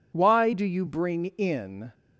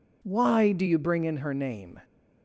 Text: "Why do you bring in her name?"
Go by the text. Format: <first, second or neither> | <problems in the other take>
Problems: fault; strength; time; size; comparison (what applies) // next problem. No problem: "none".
second | stops before "her name"; at 1.9 s